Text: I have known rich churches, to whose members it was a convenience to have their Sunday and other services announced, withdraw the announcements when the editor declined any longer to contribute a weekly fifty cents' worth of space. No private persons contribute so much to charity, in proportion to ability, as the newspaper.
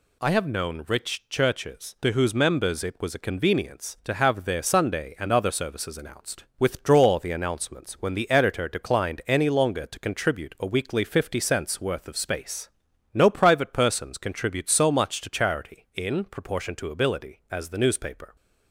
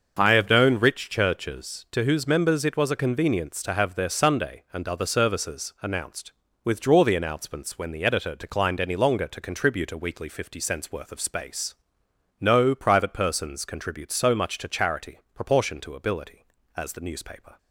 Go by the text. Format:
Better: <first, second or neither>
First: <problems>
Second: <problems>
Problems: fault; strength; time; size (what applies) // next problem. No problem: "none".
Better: first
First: none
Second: starts louder than the rest; until 1.2 s; 6.5 dB // skips "in"; at 15.2 s